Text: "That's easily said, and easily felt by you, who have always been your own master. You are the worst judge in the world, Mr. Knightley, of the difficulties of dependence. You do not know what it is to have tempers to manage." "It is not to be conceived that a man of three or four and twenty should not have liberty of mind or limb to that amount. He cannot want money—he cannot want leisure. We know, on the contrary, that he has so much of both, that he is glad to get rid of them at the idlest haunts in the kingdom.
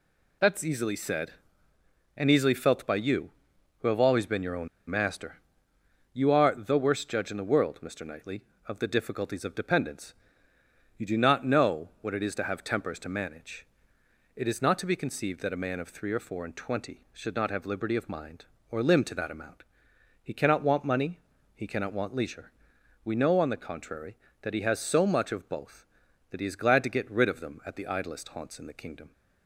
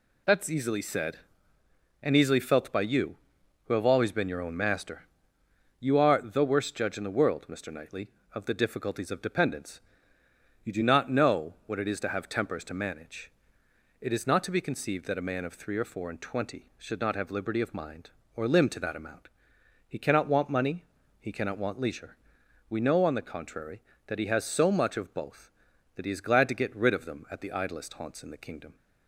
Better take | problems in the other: second | pauses between "own" and "master"; slight; at 4.6 s; 0.21 s long

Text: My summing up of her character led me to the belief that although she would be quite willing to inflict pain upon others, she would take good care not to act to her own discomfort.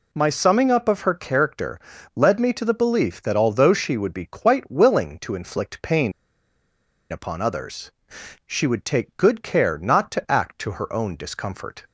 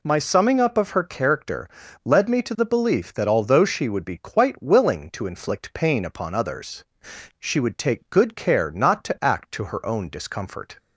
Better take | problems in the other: second | pauses between "character" and "led"; slight; at 1.7 s; 0.36 s long; slight in the second // pauses between "pain" and "upon"; at 6.1 s; 0.98 s long

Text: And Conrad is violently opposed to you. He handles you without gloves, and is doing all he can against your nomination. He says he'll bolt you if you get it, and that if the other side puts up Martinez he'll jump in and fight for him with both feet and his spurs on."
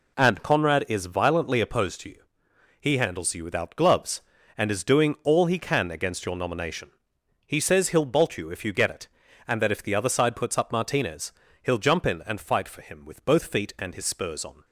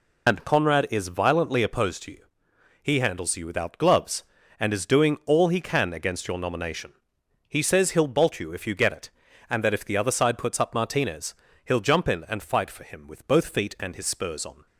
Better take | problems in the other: first | loses the start of "And"; at 0.2 s; 95 ms // pauses between "Martinez" and "he'll"; slight; at 11.3 s; 0.30 s long; slight in the first

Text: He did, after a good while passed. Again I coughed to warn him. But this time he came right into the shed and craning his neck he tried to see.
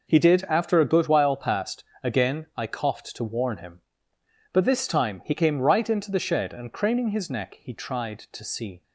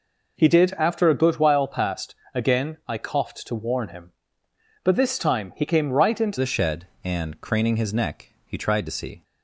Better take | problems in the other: first | changes voice at "the"; from 6.3 s on; 2.9 s long // pauses between "neck" and "he"; slight; at 8.3 s; 0.16 s long

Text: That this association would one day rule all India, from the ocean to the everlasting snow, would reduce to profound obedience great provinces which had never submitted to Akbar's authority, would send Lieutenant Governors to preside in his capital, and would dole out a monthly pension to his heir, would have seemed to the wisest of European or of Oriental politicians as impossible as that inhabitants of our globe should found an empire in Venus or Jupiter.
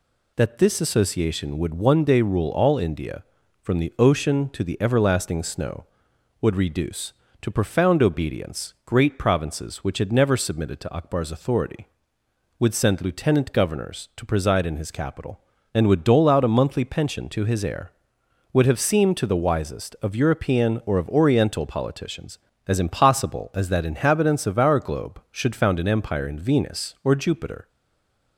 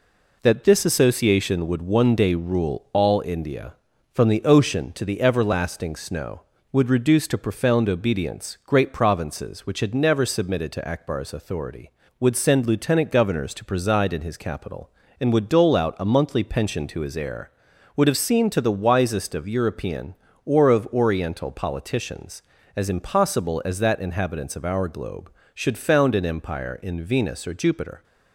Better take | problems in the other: second | stays silent after the last word; slight; from 27.6 s on; 0.7 s long

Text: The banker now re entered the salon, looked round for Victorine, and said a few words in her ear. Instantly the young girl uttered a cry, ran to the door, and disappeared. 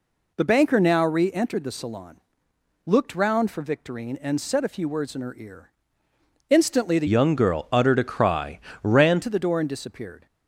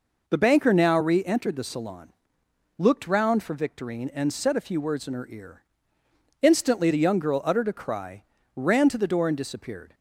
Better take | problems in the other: second | changes voice from "young" to "ran"; from 7.0 to 9.2 s; 2.2 s long

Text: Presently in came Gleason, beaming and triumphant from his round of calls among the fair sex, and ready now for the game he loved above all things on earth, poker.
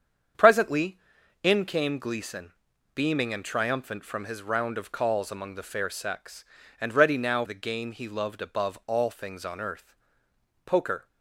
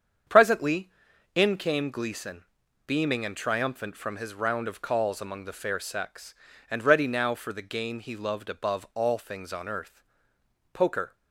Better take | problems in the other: second | starts louder than the rest; strong; until 1.8 s; 7.5 dB; strong in the second // skips "for"; at 7.4 s

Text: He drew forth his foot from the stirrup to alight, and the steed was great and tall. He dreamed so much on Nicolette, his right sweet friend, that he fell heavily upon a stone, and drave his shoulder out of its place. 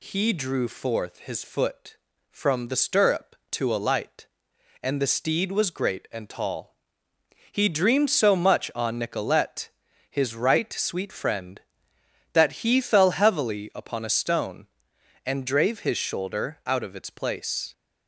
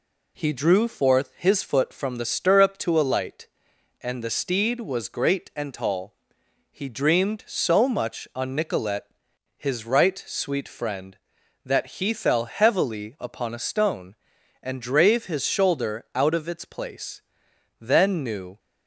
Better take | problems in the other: first | goes on to say "Then knew"; noticeable; from 17.7 s on; 0.80 s long

